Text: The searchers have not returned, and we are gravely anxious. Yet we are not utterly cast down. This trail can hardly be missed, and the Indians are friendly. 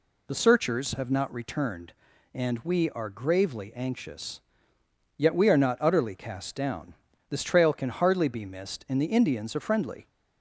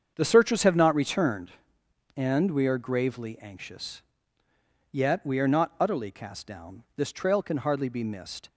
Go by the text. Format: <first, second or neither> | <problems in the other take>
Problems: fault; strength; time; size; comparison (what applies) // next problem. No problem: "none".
first | starts louder than the rest; strong; until 1.1 s; 7.5 dB // stops before "and the Indians are friendly"; at 8.4 s